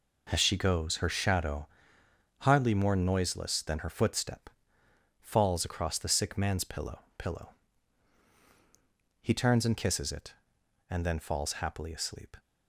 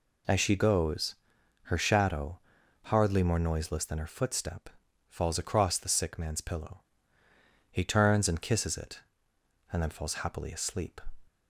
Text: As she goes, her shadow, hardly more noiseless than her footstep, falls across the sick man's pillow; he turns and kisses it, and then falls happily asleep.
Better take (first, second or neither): second